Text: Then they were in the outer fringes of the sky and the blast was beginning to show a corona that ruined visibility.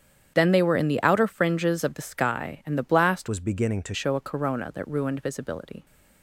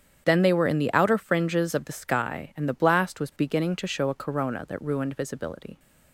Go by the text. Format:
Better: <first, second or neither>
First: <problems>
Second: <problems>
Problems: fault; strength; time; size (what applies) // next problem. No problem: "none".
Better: second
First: starts louder than the rest; strong; until 1.3 s; 9.5 dB // changes voice from "was" to "to"; from 3.2 to 3.9 s; 0.7 s long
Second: starts louder than the rest; strong; until 1.2 s; 8.5 dB